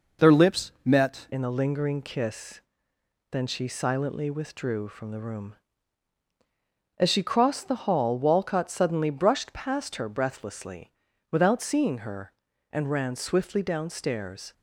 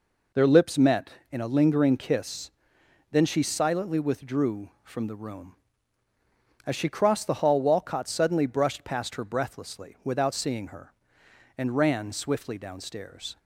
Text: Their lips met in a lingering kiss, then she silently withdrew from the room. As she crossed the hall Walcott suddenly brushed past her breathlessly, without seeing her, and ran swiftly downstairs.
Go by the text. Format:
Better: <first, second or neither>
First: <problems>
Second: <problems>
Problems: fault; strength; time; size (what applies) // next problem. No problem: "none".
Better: second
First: changes voice at "in"; from 1.3 s on; 13.2 s long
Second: none